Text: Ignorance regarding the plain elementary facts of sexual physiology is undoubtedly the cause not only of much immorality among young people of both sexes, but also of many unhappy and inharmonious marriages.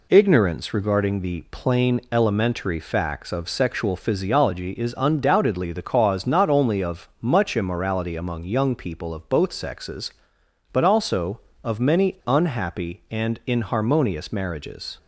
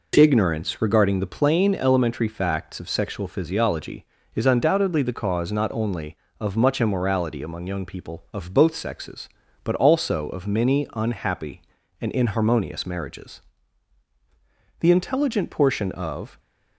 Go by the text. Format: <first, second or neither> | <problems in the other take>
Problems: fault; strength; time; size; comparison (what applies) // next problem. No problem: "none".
first | goes on to say "The intelligent portion of"; from 14.7 s on; 1.6 s long